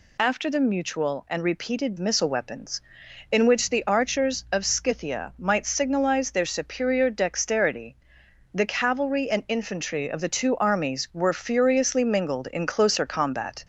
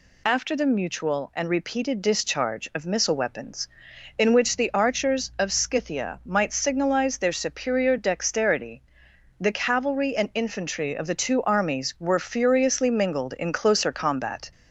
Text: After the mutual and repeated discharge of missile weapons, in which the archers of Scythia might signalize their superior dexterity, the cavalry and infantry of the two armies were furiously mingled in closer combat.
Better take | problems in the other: second | skips "discharge of"; at 1.9 s

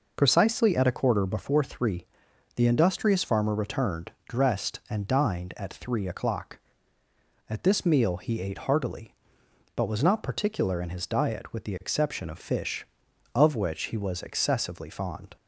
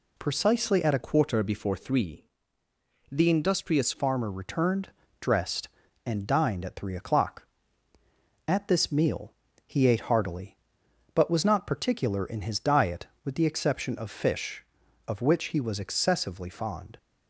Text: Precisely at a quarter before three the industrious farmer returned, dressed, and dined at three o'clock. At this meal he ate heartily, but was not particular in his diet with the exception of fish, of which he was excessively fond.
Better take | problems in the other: first | changes voice from "quarter" to "industrious"; from 1.0 to 3.9 s; 2.9 s long // pauses between "three" and "the"; noticeable; at 2.2 s; 0.88 s long; noticeable in the first // pauses between "meal" and "he"; slight; at 9.3 s; 0.34 s long

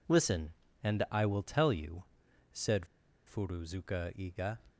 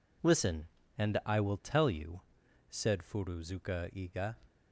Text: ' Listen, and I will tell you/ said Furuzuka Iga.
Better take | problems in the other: second | pauses between "said" and "Furuzuka"; at 2.8 s; 0.40 s long

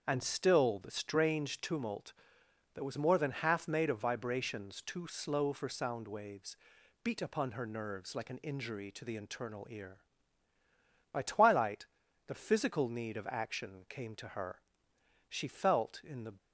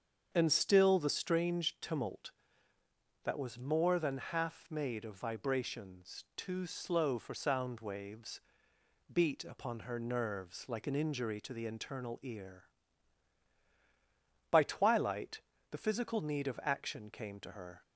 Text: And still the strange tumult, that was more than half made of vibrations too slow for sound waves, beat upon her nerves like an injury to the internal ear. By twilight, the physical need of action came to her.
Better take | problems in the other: second | starts louder than the rest; until 1.0 s; 6.5 dB; also in the second // goes on to say "She felt in the"; noticeable; from 15.3 s on; 1.0 s long

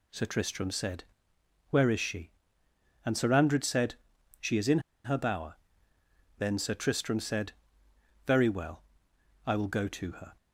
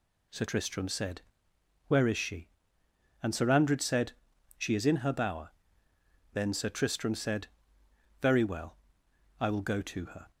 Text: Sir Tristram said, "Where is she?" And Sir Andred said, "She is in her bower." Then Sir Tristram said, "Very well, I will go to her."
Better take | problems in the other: second | pauses between "in" and "her"; slight; at 4.7 s; 0.25 s long

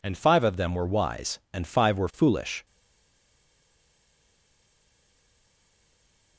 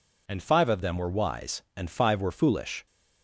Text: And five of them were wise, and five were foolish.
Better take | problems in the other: second | stays silent after the last word; strong; from 2.6 s on; 3.7 s long

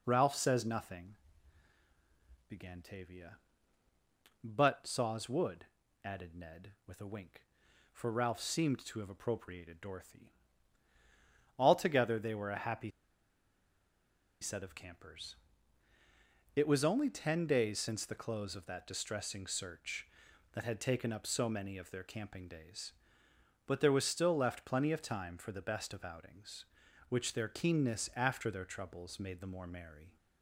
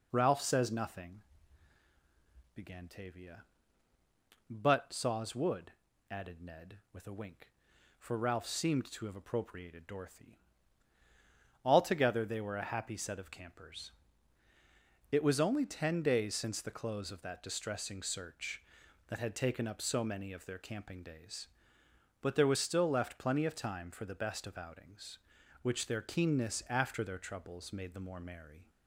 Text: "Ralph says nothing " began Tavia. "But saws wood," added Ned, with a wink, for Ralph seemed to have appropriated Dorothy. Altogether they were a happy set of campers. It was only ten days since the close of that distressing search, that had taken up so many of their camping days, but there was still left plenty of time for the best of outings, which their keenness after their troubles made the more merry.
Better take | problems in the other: second | pauses between "happy" and "set"; strong; at 12.8 s; 1.5 s long

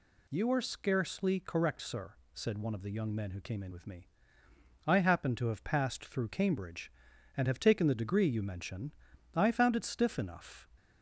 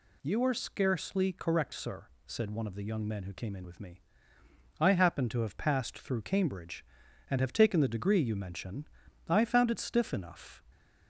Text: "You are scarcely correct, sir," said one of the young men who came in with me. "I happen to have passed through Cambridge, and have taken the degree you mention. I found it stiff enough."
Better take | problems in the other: neither | none

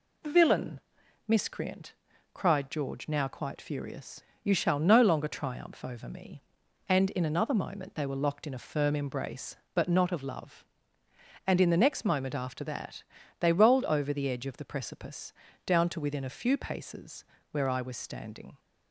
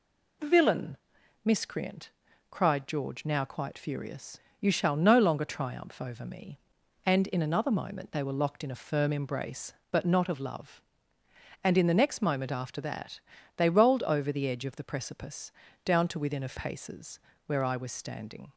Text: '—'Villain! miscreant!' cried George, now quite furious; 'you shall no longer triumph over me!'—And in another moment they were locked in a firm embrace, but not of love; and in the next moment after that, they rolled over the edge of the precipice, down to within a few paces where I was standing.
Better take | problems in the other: first | skips "few"; at 16.5 s // pauses between "paces" and "where"; slight; at 17.1 s; 0.26 s long; slight in the first

